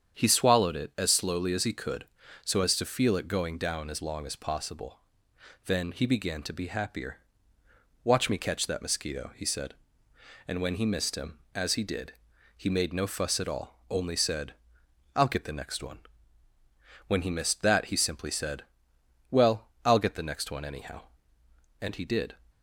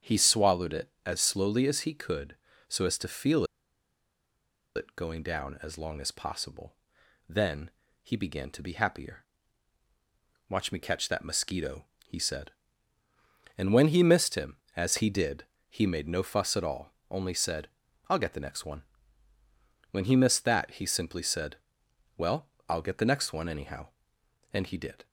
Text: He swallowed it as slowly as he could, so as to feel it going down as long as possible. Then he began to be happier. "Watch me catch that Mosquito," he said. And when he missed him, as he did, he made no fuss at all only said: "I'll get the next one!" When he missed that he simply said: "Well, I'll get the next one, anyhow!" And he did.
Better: first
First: starts louder than the rest; strong; until 1.2 s; 8 dB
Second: starts louder than the rest; strong; until 1.1 s; 8 dB // pauses between "feel" and "it"; strong; at 3.4 s; 1.3 s long // pauses between "Then" and "he"; slight; at 7.6 s; 0.32 s long // pauses between "all" and "only"; slight; at 16.9 s; 0.18 s long

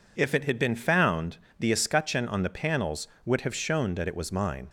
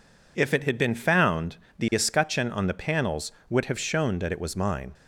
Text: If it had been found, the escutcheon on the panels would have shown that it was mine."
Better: neither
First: none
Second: none

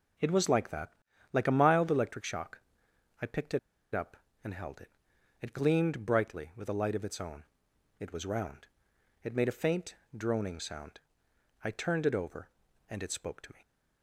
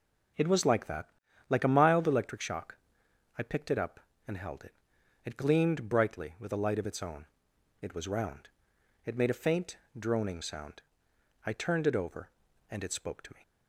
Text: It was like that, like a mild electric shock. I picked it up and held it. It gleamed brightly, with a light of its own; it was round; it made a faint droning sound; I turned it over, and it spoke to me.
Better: second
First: pauses between "it" and "up"; slight; at 3.5 s; 0.35 s long // pauses between "faint" and "droning"; slight; at 9.9 s; 0.20 s long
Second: pauses between "faint" and "droning"; slight; at 9.7 s; 0.20 s long

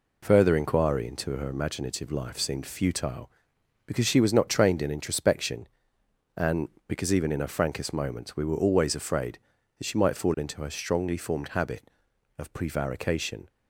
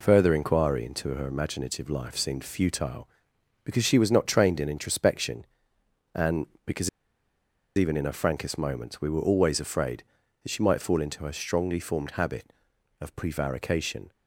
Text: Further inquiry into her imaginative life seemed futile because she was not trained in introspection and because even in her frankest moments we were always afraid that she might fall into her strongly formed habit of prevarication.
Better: first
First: none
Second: pauses between "because" and "even"; noticeable; at 6.8 s; 0.89 s long

